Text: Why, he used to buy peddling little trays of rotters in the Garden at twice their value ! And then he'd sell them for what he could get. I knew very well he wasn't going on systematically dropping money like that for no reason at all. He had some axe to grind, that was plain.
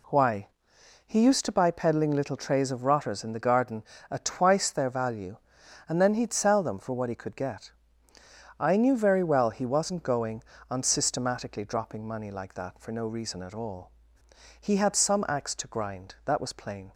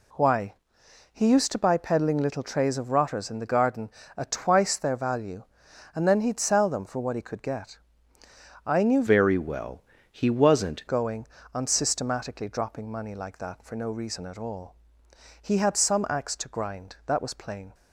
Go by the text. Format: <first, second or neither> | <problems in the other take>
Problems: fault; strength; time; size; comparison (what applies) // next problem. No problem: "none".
first | changes voice from "very" to "wasn't"; from 9.0 to 10.8 s; 1.8 s long // pauses between "well" and "he"; slight; at 9.8 s; 0.28 s long